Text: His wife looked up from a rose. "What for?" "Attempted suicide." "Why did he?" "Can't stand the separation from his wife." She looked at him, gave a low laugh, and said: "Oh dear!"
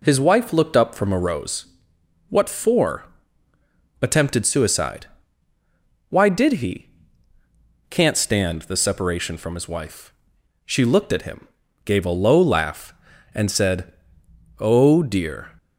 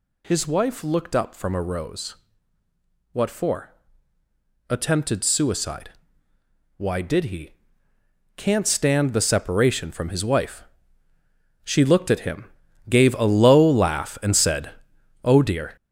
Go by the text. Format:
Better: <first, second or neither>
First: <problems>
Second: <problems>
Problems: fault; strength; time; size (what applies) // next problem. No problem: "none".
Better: first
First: none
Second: gets louder; strong; throughout; 8 dB